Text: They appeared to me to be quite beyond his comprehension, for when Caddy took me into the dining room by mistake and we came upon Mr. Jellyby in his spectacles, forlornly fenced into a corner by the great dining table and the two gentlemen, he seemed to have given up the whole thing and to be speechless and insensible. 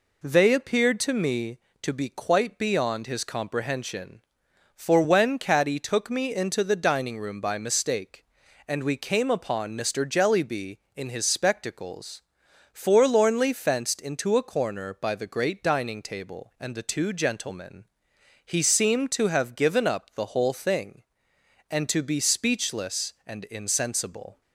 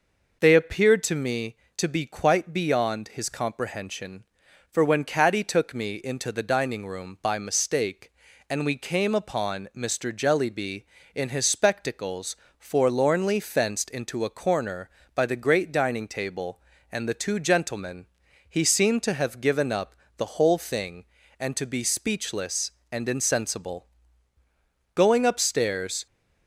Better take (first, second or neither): first